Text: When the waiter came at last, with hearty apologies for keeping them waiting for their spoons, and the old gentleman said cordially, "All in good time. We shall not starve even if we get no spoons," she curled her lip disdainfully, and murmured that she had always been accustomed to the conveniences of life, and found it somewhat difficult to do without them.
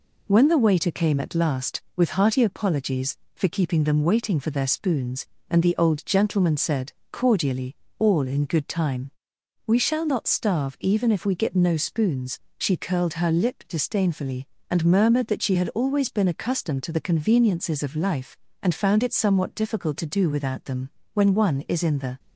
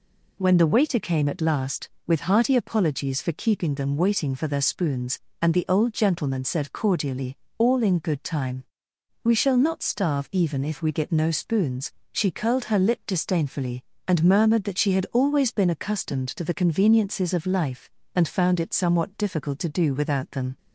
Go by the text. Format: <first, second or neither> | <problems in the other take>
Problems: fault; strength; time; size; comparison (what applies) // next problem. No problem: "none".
second | pauses between "said" and "cordially"; slight; at 6.9 s; 0.20 s long // goes on to say "When one is in the"; noticeable; from 21.1 s on; 1.0 s long